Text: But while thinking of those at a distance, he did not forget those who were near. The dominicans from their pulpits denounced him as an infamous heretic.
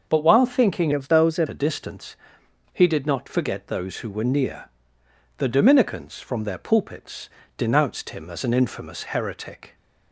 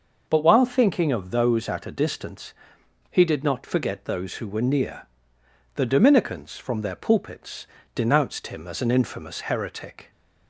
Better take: second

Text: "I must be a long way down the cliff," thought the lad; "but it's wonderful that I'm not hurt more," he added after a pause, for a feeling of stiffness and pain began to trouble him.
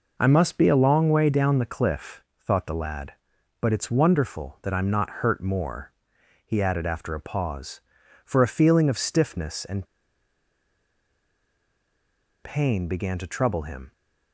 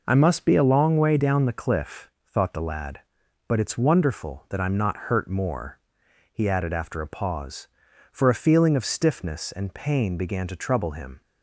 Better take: second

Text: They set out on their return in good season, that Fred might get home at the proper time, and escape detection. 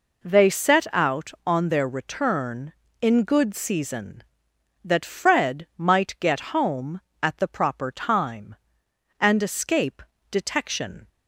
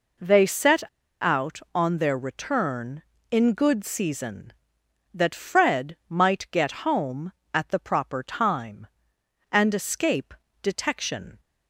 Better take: first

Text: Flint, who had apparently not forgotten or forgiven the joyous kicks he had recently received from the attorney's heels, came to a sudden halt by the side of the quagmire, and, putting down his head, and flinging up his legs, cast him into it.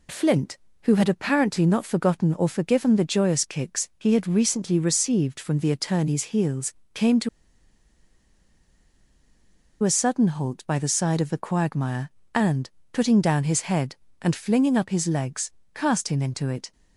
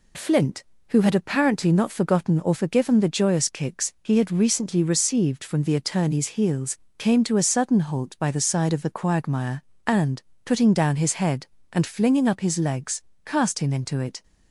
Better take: second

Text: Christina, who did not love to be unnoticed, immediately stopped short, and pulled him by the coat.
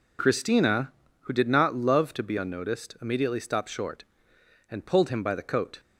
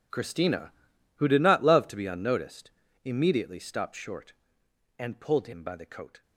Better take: first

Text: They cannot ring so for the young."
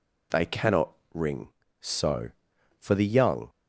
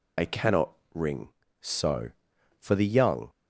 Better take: first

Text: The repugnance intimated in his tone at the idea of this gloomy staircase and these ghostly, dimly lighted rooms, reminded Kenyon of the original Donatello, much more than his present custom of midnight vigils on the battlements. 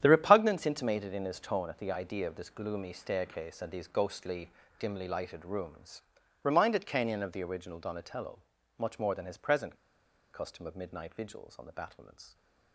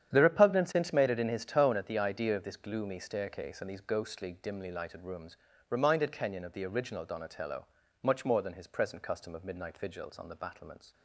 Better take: second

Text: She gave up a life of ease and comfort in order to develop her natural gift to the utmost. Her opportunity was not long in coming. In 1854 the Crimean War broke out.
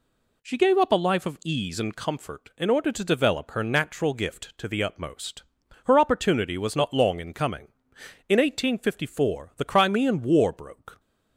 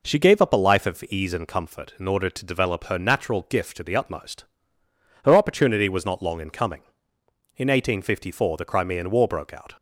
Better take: second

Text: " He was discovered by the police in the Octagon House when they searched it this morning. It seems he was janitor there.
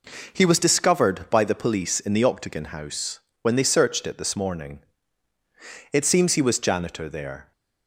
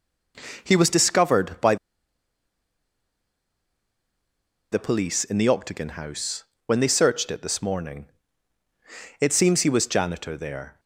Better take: first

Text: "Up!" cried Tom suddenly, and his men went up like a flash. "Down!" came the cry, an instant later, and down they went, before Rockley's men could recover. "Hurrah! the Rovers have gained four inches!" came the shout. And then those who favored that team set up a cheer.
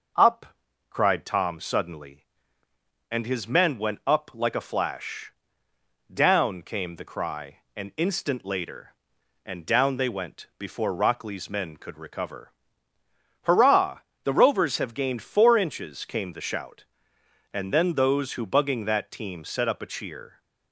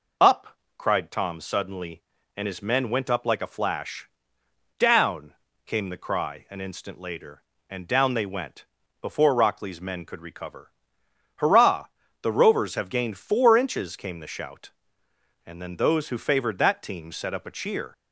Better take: second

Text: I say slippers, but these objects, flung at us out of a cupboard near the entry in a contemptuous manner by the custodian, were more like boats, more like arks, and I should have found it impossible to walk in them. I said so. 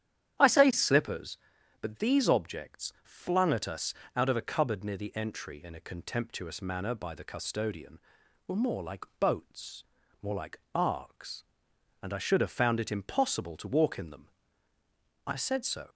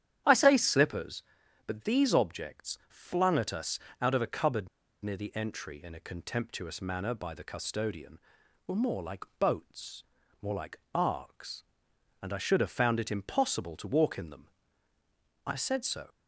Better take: first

